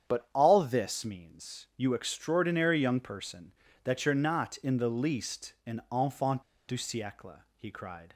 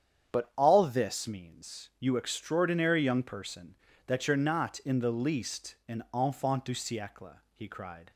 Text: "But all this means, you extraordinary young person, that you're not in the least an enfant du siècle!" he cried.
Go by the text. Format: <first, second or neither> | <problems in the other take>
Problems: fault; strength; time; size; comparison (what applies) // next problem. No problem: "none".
second | starts louder than the rest; strong; until 1.1 s; 8.5 dB; strong in the second // pauses between "enfant" and "du"; slight; at 6.4 s; 0.26 s long